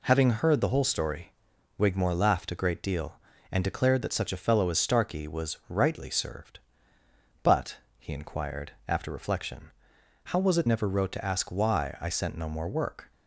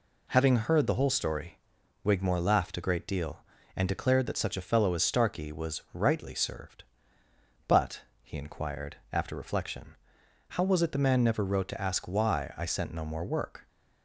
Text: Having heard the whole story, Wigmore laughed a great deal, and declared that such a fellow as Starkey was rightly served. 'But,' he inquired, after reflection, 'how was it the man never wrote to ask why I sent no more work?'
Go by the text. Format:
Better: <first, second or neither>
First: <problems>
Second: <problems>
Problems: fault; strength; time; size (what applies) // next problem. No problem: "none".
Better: second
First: skips "the man"; at 10.6 s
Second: none